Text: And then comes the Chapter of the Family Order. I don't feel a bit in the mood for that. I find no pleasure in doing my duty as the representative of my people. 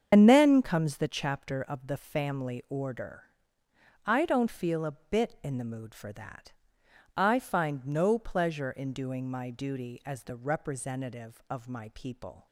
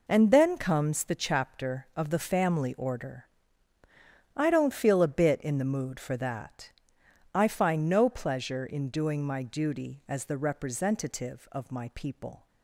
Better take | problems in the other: second | loses the start of "And"; at 0.1 s; 65 ms // starts louder than the rest; strong; until 1.1 s; 7.5 dB

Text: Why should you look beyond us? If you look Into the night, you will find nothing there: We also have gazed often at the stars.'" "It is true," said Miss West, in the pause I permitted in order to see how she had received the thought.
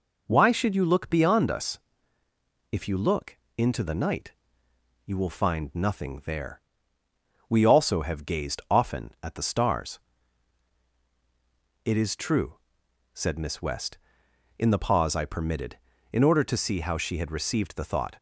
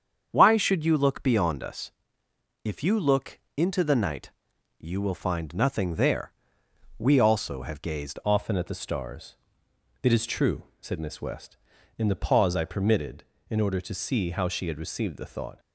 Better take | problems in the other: first | starts louder than the rest; strong; until 1.3 s; 7.5 dB // pauses between "look" and "Into"; slight; at 3.3 s; 0.20 s long; slight in the first // changes voice at "often"; from 8.2 s on; 7.3 s long

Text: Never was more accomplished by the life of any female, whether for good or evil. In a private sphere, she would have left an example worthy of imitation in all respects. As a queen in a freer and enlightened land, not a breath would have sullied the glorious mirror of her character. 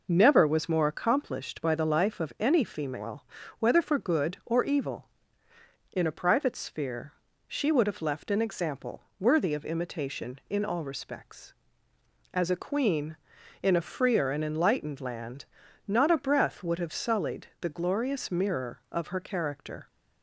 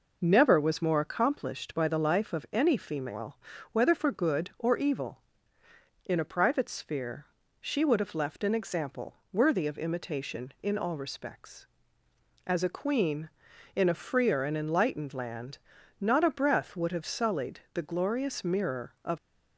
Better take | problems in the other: first | pauses between "sullied" and "the"; slight; at 17.5 s; 0.16 s long; slight in the first // stops before "her character"; at 19.1 s

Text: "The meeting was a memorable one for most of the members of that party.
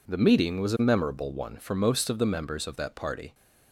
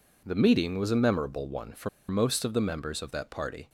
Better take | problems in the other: first | pauses between "for" and "most"; slight; at 1.8 s; 0.20 s long

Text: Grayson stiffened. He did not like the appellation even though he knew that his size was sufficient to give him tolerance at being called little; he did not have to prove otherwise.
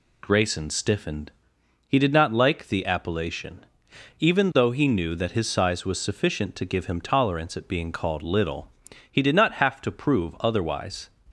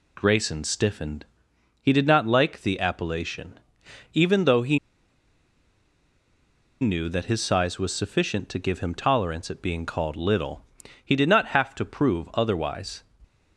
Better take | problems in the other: first | pauses between "appellation" and "even"; noticeable; at 3.6 s; 0.52 s long; noticeable in the first // pauses between "he" and "knew"; strong; at 4.7 s; 2.0 s long

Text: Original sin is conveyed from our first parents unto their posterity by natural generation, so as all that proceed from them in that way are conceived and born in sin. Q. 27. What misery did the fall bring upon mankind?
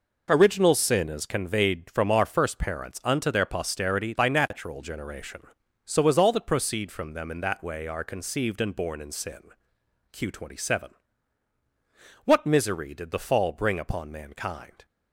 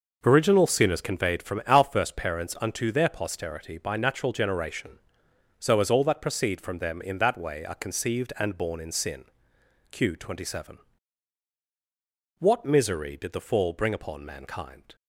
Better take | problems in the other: neither | none

